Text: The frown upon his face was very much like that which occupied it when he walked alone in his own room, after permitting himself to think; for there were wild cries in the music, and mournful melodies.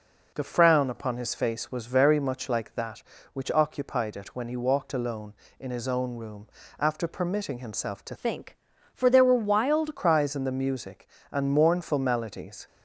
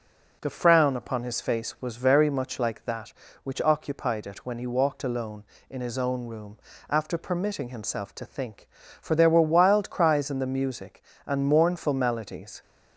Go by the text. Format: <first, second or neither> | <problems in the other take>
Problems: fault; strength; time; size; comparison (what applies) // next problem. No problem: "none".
second | changes voice from "think" to "wild"; from 8.1 to 9.9 s; 1.8 s long